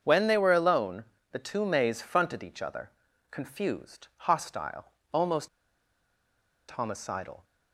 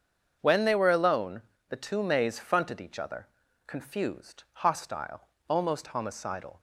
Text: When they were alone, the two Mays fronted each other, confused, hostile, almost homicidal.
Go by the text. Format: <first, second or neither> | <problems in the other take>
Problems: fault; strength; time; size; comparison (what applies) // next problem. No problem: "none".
second | starts louder than the rest; until 1.0 s; 7 dB; strong in the second // pauses between "almost" and "homicidal"; at 5.4 s; 1.2 s long